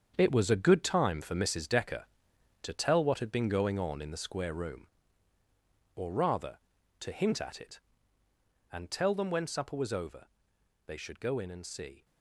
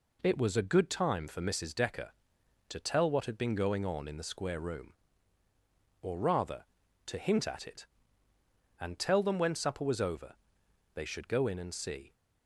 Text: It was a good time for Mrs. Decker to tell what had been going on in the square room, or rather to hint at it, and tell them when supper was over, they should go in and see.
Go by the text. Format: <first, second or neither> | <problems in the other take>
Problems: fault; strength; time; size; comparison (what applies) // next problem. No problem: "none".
second | gets quieter; strong; throughout; 10 dB